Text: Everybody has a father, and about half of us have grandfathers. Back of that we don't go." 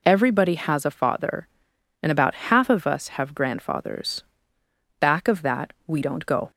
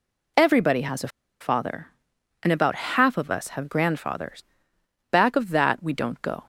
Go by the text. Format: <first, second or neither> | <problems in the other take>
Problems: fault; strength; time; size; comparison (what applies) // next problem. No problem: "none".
first | pauses between "a" and "father"; slight; at 1.0 s; 0.32 s long